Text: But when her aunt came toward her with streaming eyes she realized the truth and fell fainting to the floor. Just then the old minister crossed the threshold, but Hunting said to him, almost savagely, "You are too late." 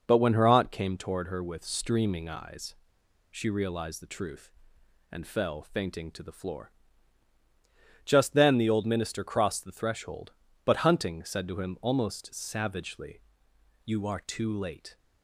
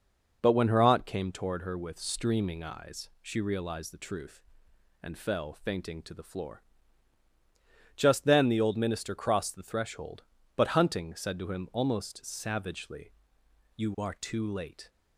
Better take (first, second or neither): second